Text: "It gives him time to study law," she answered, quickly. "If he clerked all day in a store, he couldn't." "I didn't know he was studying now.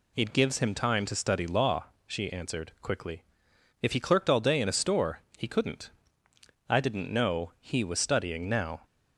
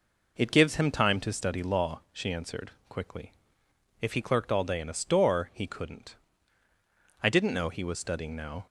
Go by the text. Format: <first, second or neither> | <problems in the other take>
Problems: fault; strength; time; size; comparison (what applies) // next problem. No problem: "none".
neither | none